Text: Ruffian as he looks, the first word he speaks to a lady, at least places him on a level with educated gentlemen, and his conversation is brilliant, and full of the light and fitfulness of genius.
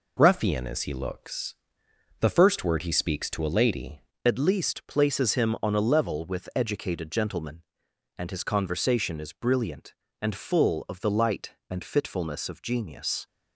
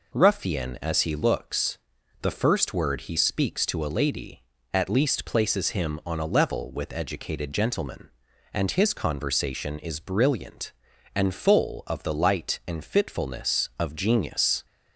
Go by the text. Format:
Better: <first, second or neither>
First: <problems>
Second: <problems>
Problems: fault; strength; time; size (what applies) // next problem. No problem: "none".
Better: second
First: changes voice at "at"; from 4.2 s on; 9.0 s long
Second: none